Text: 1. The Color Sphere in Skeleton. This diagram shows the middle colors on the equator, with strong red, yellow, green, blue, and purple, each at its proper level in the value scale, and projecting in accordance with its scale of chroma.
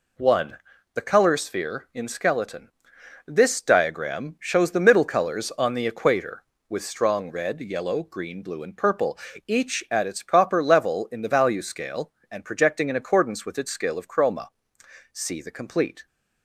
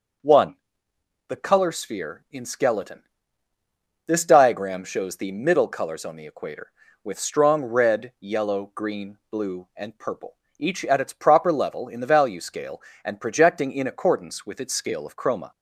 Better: second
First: goes on to say "See the complete"; noticeable; from 15.1 s on; 0.94 s long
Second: none

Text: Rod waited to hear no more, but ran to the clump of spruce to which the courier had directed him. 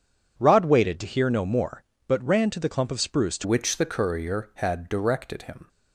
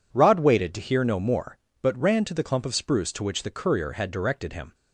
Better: second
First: changes voice at "which"; from 3.4 s on; 2.2 s long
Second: none

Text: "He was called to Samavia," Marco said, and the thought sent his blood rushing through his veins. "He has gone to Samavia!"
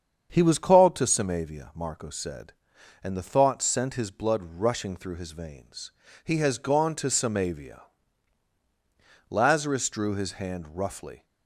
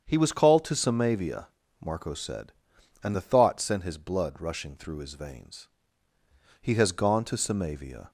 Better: second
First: starts louder than the rest; strong; until 1.3 s; 7.5 dB // goes on to say "Lazarus drew his hand roughly"; strong; from 9.2 s on; 1.9 s long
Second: starts louder than the rest; strong; until 1.0 s; 7.5 dB

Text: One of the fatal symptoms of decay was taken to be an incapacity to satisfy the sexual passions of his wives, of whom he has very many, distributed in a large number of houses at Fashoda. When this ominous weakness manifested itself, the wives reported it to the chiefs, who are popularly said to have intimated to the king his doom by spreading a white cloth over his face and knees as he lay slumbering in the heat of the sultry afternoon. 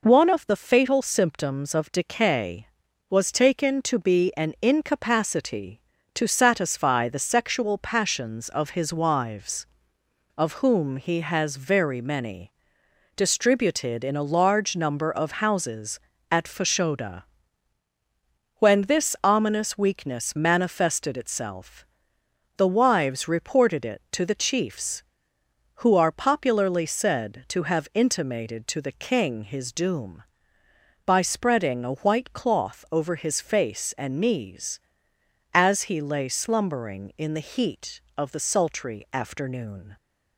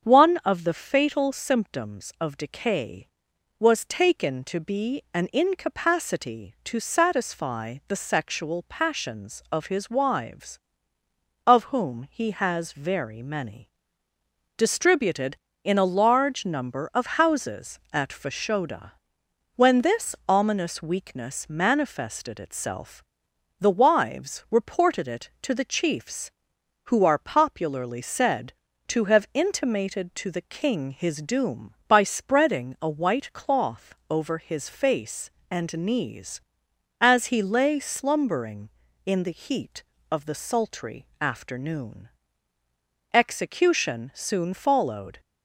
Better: first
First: none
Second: starts louder than the rest; strong; until 1.1 s; 7.5 dB // pauses between "cloth" and "over"; slight; at 33.9 s; 0.16 s long // goes on to say "Execution soon followed"; strong; from 43.1 s on; 2.0 s long

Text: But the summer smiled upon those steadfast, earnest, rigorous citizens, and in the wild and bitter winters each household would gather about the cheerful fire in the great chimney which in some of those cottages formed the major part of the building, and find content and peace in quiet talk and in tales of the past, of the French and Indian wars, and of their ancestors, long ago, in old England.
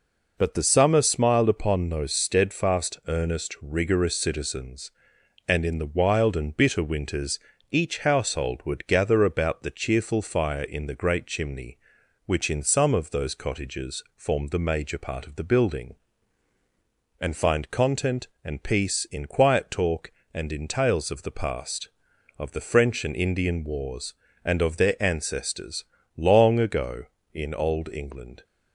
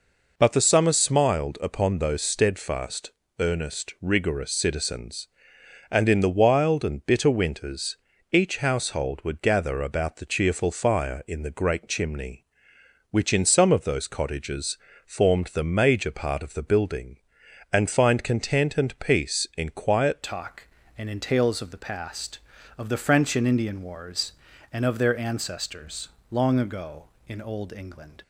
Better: first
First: pauses between "winters" and "each"; slight; at 7.3 s; 0.32 s long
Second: pauses between "winters" and "each"; slight; at 7.9 s; 0.34 s long // pauses between "cottages" and "formed"; slight; at 14.7 s; 0.30 s long // changes voice at "talk"; from 20.2 s on; 8.0 s long

